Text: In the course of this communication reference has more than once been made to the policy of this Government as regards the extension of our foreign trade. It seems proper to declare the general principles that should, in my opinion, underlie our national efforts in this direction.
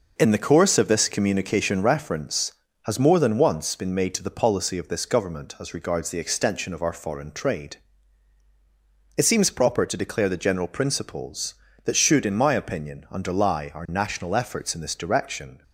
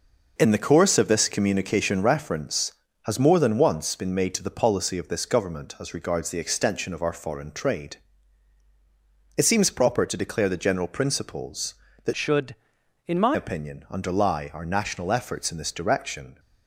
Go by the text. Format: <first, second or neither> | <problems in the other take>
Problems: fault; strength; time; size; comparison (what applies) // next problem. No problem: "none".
first | changes voice from "should" to "my"; from 12.1 to 13.3 s; 1.2 s long